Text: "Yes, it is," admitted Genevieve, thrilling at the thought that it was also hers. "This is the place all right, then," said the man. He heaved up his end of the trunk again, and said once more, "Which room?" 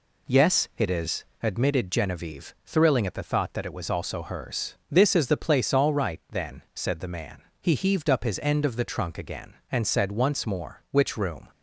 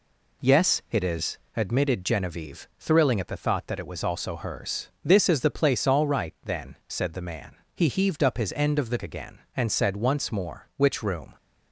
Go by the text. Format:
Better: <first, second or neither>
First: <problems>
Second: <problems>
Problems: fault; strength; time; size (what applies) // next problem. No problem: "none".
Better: first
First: none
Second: skips "trunk"; at 9.0 s